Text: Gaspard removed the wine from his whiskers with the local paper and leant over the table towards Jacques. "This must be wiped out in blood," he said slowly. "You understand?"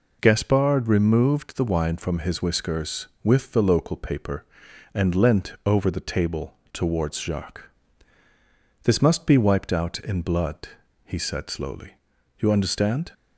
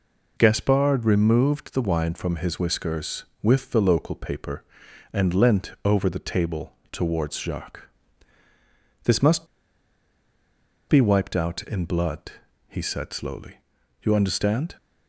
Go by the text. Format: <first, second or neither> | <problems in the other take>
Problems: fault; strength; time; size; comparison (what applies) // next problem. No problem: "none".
first | pauses between "table" and "towards"; slight; at 6.7 s; 0.16 s long; slight in the first // pauses between "must" and "be"; strong; at 9.4 s; 1.4 s long